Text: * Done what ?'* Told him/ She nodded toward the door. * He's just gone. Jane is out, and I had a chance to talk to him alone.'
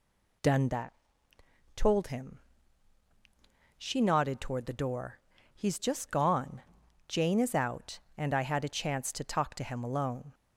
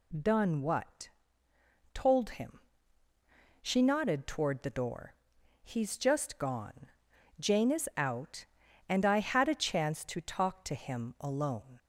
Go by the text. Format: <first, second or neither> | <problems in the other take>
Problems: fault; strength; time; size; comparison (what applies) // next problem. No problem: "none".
second | says "that" for "what"; at 0.6 s